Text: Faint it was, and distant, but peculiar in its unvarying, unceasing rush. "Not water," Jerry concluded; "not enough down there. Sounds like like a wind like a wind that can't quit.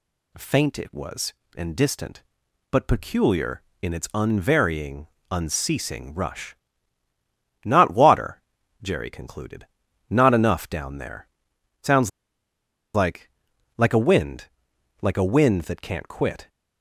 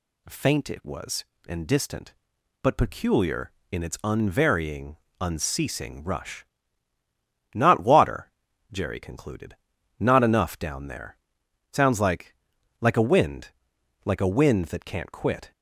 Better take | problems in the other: second | pauses between "Sounds" and "like"; noticeable; at 12.0 s; 0.84 s long // pauses between "like" and "like"; noticeable; at 13.2 s; 0.48 s long; noticeable in the second // pauses between "wind" and "like"; noticeable; at 14.4 s; 0.54 s long; noticeable in the second

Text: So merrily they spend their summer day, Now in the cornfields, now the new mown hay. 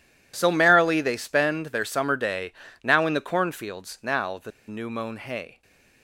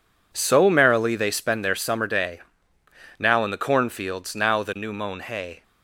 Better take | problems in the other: second | pauses between "the" and "new"; slight; at 4.5 s; 0.17 s long

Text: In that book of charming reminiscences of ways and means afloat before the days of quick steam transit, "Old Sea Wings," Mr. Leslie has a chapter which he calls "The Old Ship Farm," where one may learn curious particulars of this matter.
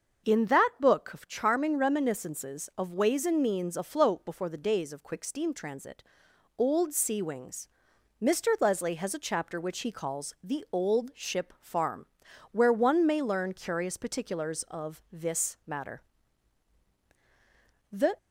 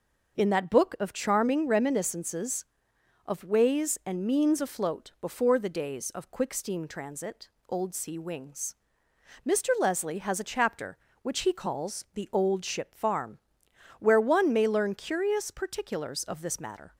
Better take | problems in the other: second | starts louder than the rest; until 1.3 s; 6.5 dB // goes on to say "The"; slight; from 17.9 s on; 0.26 s long

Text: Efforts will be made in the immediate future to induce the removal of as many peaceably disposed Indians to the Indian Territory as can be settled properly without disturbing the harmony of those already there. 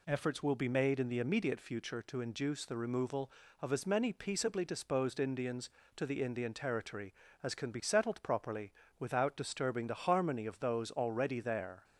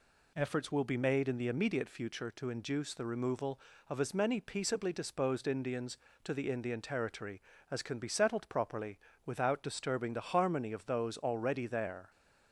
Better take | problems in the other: neither | pauses between "properly" and "without"; slight; the same in both

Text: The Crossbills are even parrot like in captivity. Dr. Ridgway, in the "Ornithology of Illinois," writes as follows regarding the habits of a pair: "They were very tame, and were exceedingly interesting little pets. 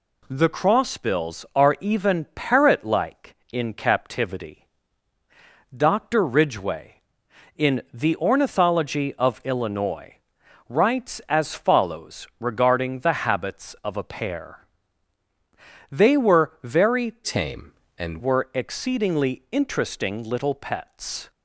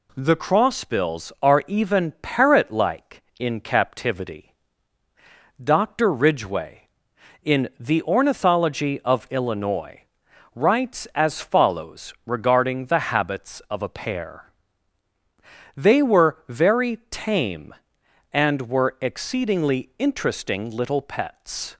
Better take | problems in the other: second | changes voice from "tame" to "and"; from 17.2 to 18.2 s; 1.0 s long

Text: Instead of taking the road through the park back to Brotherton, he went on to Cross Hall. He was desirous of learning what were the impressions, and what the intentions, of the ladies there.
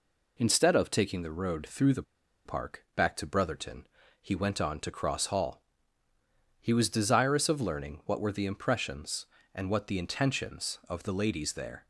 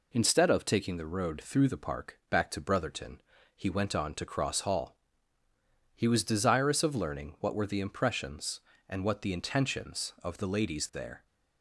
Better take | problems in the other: second | pauses between "the" and "park"; at 2.0 s; 0.42 s long

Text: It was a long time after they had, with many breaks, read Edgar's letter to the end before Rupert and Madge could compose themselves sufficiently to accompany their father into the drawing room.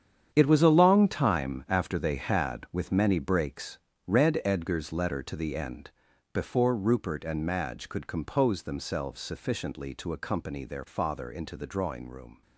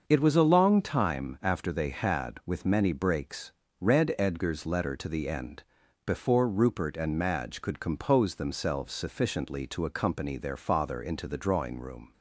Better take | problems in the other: second | gets quieter; strong; throughout; 11.5 dB // starts louder than the rest; strong; until 1.3 s; 8.5 dB; also in the second // pauses between "end" and "before"; at 5.8 s; 0.42 s long; also in the second

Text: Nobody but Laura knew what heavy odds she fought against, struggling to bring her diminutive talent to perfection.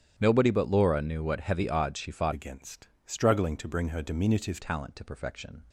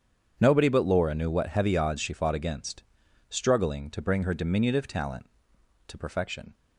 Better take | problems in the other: second | starts louder than the rest; strong; until 1.1 s; 9.5 dB; strong in the second // changes voice from "against" to "diminutive"; from 2.3 to 4.6 s; 2.3 s long

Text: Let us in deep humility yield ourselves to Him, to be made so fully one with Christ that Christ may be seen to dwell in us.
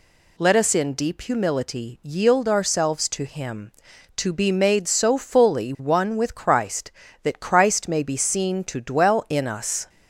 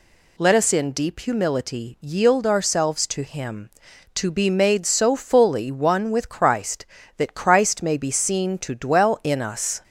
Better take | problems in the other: neither | none

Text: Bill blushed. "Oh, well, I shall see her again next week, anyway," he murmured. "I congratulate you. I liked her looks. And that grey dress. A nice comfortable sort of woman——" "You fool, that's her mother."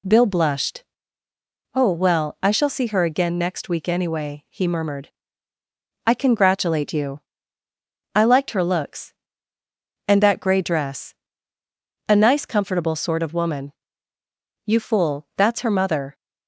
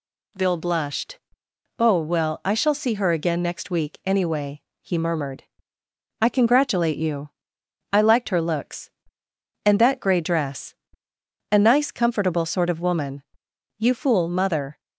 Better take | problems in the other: first | skips "that's her"; at 14.2 s

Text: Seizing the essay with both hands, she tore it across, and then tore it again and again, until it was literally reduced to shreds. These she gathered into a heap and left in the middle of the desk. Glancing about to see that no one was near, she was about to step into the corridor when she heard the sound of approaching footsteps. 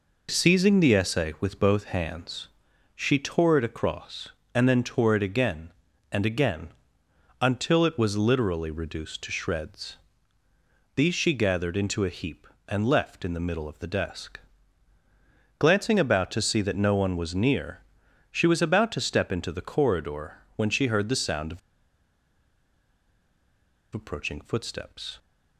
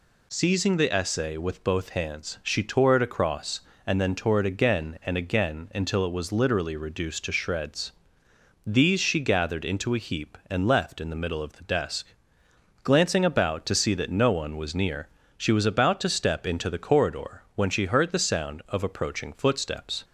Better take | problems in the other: second | pauses between "corridor" and "when"; slight; at 20.3 s; 0.18 s long // pauses between "of" and "approaching"; strong; at 21.5 s; 2.3 s long

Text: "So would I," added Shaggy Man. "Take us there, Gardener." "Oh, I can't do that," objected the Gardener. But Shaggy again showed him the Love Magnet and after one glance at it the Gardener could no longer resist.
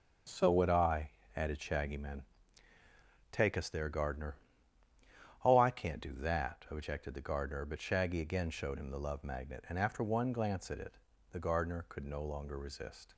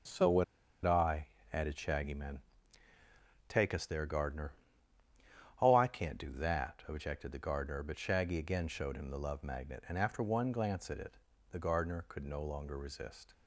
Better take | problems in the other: first | starts louder than the rest; strong; until 1.7 s; 7 dB; strong in the first // pauses between "would" and "I"; at 0.4 s; 0.40 s long // pauses between "it" and "the"; slight; at 11.1 s; 0.34 s long; slight in the first

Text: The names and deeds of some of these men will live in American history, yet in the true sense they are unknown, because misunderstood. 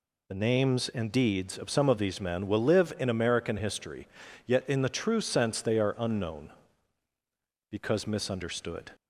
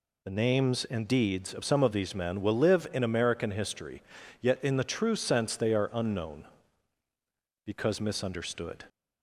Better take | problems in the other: neither | none

